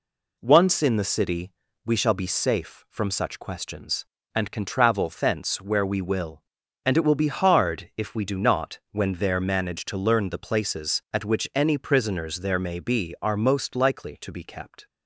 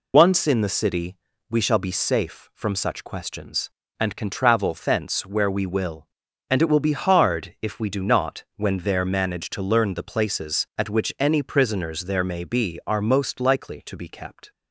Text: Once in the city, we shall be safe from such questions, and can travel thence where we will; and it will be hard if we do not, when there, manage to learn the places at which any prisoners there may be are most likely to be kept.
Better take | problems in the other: first | loses the start of "Once"; at 0.1 s; 95 ms

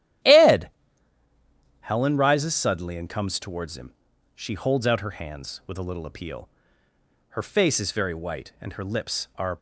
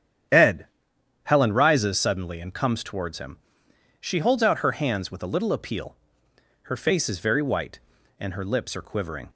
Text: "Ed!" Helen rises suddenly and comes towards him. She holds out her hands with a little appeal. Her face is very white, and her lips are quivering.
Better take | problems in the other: second | starts louder than the rest; strong; until 2.3 s; 12.5 dB; strong in the second // stops before "quivering"; at 9.5 s

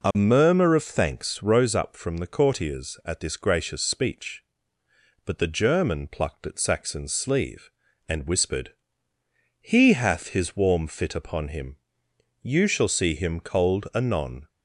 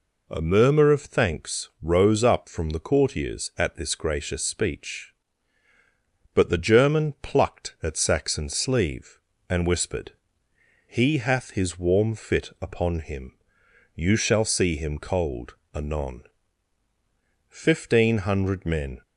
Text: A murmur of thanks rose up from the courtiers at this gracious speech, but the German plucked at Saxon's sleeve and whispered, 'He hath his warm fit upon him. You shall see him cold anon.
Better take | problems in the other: first | pauses between "cold" and "anon"; slight; at 15.5 s; 0.18 s long // goes on to say "Fifteen hundred men"; from 17.4 s on; 1.5 s long

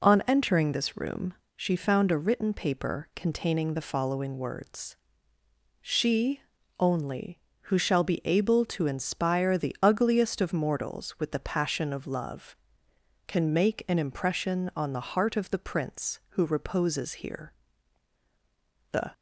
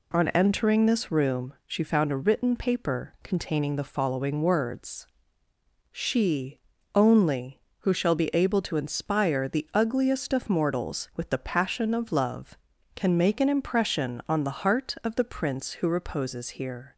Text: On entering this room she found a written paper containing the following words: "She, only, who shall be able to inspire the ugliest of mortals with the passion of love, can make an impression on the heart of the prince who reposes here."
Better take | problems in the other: second | pauses between "room" and "she"; slight; at 1.3 s; 0.22 s long // goes on to say "The"; slight; from 18.9 s on; 0.22 s long

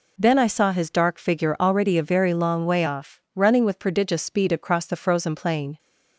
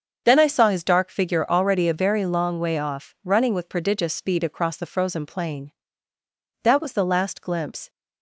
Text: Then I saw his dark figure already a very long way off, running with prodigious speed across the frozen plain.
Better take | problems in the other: first | starts louder than the rest; until 1.2 s; 7 dB // goes on to say "That was the last glimpse"; noticeable; from 6.6 s on; 1.2 s long

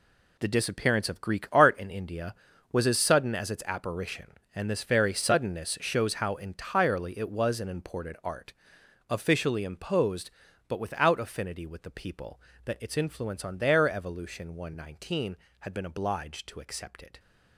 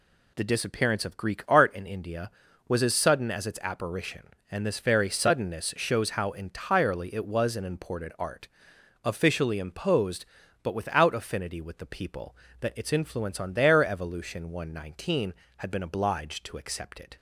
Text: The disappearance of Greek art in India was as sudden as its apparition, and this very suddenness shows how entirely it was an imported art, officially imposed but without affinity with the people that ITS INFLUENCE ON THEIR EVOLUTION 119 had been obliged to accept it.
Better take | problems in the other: second | gets quieter; strong; throughout; 10.5 dB

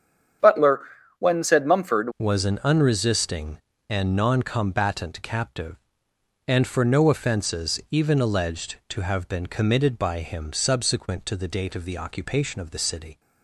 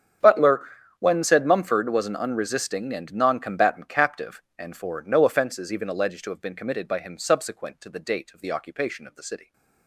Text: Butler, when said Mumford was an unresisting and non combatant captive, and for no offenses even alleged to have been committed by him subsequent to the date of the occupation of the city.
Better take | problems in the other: second | starts louder than the rest; strong; until 1.7 s; 8.5 dB; strong in the second // changes voice at "was"; from 2.1 s on; 11.0 s long

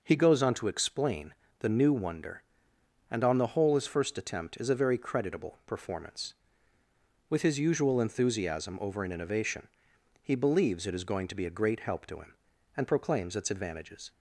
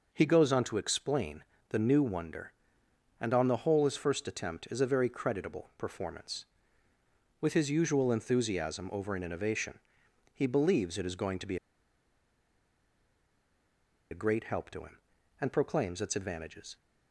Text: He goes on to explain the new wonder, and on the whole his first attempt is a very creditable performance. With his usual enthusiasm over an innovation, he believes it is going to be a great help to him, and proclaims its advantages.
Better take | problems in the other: first | pauses between "explain" and "the"; slight; at 1.4 s; 0.26 s long; slight in the first // pauses between "be" and "a"; strong; at 11.5 s; 2.5 s long

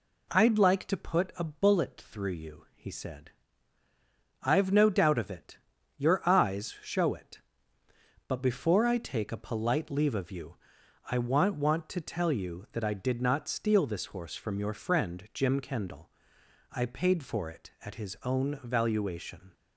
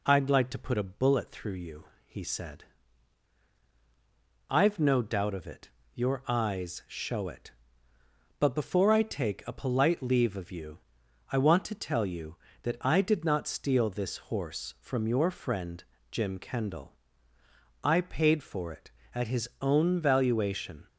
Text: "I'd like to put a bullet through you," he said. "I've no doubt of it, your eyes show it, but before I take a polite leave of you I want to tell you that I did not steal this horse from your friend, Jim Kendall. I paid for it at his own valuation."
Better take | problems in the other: second | pauses between "you" and "I"; noticeable; at 10.5 s; 0.54 s long; noticeable in the second // says "want" twice; at 11.5 s

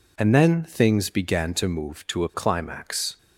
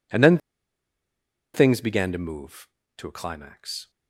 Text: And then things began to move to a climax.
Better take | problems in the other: first | pauses between "then" and "things"; at 0.3 s; 1.1 s long

